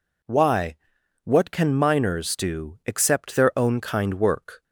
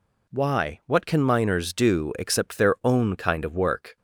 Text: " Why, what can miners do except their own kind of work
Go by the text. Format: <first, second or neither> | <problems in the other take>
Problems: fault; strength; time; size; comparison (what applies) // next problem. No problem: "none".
second | skips "of"; at 4.1 s